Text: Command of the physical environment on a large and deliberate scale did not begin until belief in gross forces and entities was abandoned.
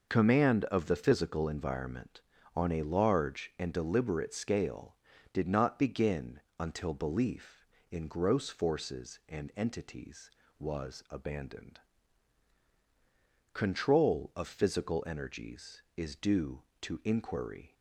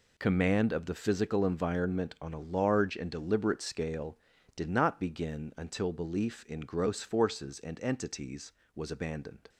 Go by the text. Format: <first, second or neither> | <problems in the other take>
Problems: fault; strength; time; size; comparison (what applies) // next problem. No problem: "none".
second | pauses between "begin" and "until"; slight; at 6.3 s; 0.18 s long // goes on to say "Control of physical energies is due to inquiry"; strong; from 13.5 s on; 4.2 s long